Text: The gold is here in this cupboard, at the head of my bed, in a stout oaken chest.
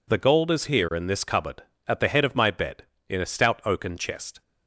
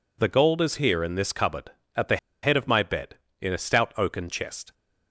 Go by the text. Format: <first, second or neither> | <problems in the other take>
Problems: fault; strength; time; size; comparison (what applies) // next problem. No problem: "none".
first | pauses between "the" and "head"; slight; at 2.1 s; 0.25 s long